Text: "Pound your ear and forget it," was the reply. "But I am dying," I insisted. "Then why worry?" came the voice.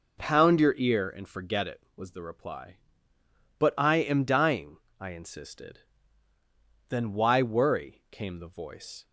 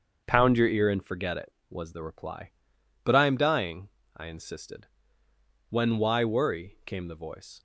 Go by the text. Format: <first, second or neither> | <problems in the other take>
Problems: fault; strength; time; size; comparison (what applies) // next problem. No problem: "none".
first | starts louder than the rest; until 1.2 s; 6.5 dB // says "When" for "Then"; at 5.6 s